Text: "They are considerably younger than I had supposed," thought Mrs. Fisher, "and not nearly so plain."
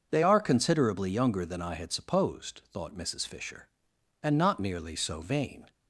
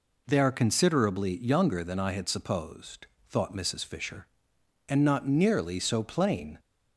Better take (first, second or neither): second